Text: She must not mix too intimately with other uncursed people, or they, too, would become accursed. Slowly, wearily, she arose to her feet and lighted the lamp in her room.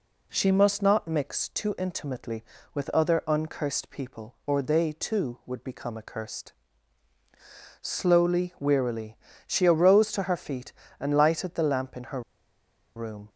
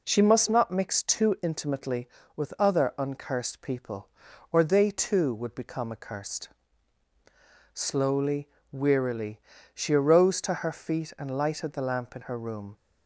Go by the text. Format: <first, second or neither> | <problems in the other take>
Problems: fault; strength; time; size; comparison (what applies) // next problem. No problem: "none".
second | pauses between "her" and "room"; noticeable; at 12.2 s; 0.75 s long